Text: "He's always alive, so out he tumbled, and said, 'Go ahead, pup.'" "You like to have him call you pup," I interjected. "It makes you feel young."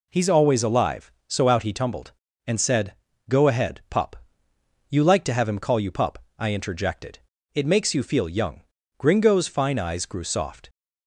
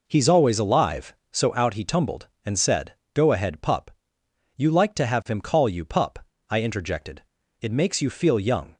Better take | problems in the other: second | goes on to say "Gringo's fine eyes grew soft"; strong; from 8.9 s on; 1.7 s long

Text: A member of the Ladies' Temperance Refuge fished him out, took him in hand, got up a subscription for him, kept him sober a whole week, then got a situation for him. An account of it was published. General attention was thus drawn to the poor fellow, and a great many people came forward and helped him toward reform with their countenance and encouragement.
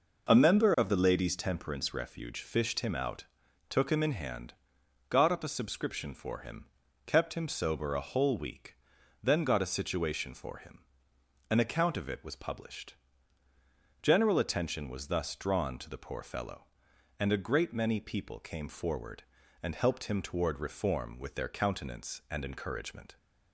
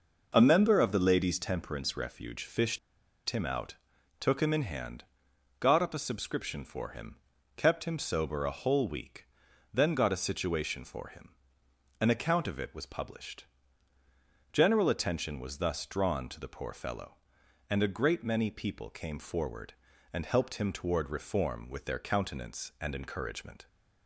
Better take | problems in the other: first | pauses between "fished" and "him"; noticeable; at 2.7 s; 0.50 s long

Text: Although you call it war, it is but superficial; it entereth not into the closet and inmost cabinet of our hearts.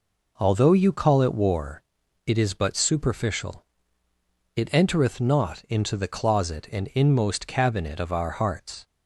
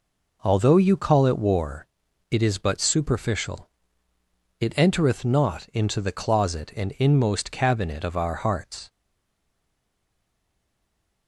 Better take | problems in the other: first | stays silent after the last word; from 8.8 s on; 2.4 s long

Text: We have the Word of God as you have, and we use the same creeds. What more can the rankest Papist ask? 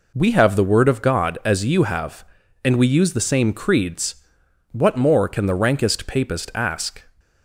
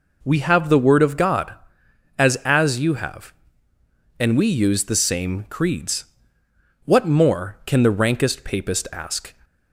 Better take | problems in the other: first | says "as" twice; at 2.4 s

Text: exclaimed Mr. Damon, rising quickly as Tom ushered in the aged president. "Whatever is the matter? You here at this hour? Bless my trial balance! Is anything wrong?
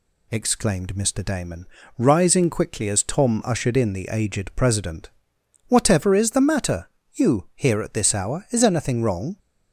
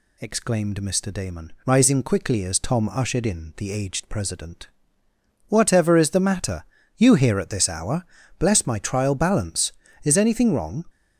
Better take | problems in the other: second | skips "Bless my trial balance"; at 8.4 s

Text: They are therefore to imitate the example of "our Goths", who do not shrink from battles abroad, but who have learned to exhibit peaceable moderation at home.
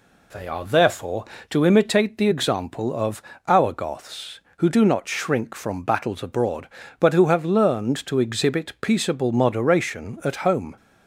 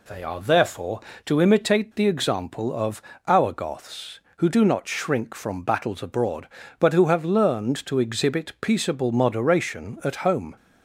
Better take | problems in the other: neither | pauses between "of" and "our"; slight; the same in both

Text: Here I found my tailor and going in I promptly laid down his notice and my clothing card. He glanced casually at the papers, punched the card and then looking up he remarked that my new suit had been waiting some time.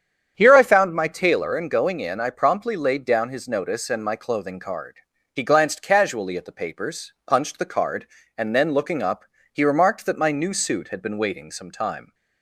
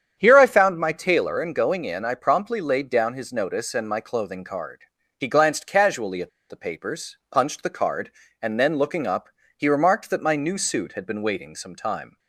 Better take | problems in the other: first | starts louder than the rest; strong; until 1.1 s; 8.5 dB; strong in the first // pauses between "at" and "the"; slight; at 6.2 s; 0.20 s long // pauses between "up" and "he"; slight; at 9.3 s; 0.26 s long; slight in the first

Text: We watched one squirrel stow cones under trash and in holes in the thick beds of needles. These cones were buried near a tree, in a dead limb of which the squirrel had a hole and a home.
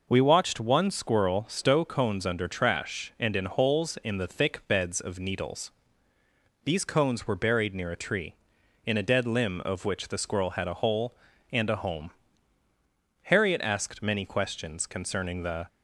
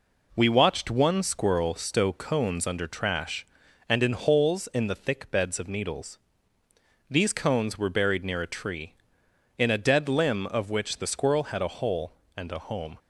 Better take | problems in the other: second | goes on to say "Harriet asked many questions concerning the"; strong; from 13.2 s on; 2.4 s long

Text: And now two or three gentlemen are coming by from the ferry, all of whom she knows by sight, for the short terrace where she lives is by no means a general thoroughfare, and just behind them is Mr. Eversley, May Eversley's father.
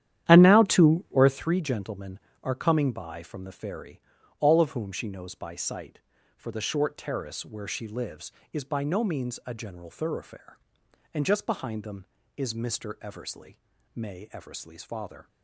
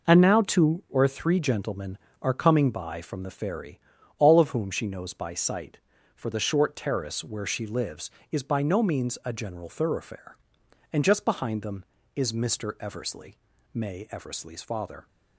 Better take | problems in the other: second | starts louder than the rest; strong; until 1.6 s; 11 dB

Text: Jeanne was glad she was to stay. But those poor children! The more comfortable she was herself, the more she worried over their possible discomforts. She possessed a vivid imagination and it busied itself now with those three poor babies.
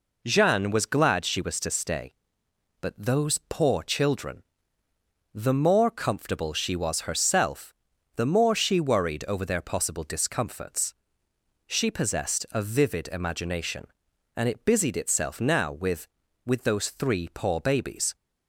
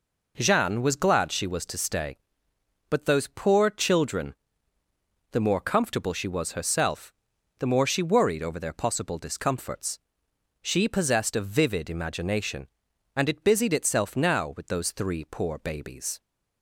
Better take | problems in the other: second | says "with" twice; at 16.4 s

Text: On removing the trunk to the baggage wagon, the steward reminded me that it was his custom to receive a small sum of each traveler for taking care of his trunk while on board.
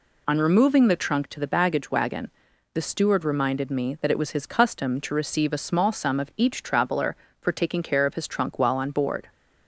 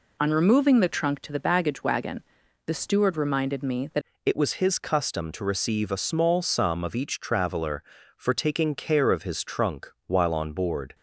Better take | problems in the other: first | changes voice at "it"; from 4.2 s on; 6.7 s long

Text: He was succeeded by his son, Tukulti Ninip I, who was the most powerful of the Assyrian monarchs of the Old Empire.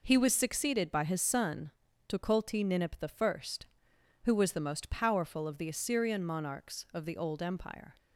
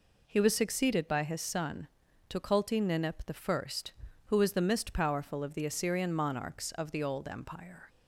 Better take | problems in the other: first | says "mist" for "most"; at 4.6 s

